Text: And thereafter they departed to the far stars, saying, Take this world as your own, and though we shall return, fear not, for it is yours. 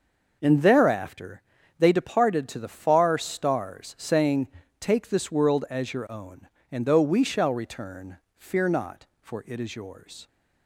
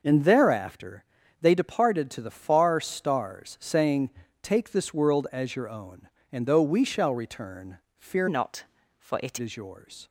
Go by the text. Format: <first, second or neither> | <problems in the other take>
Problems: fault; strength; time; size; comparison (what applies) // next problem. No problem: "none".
first | pauses between "thereafter" and "they"; at 1.0 s; 0.38 s long; also in the first // changes voice from "not" to "it"; from 8.2 to 9.3 s; 1.1 s long